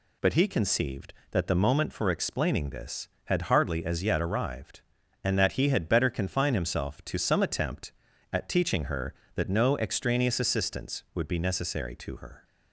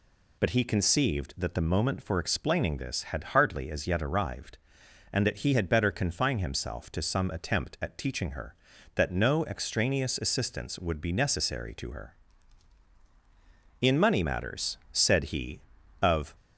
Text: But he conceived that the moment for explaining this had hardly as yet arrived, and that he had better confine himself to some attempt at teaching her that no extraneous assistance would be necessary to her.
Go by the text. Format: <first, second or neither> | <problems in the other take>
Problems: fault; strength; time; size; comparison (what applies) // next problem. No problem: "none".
first | goes on to say "In money matters said he of"; strong; from 13.8 s on; 2.5 s long